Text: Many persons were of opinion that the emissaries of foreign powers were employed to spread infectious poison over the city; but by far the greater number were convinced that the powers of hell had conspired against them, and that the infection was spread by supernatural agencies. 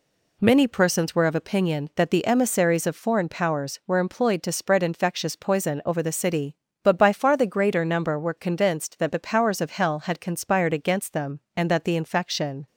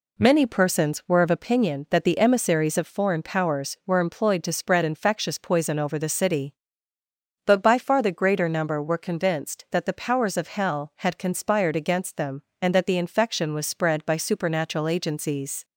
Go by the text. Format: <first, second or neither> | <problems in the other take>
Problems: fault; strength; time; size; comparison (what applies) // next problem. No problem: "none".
second | stops before "was spread by supernatural agencies"; at 12.6 s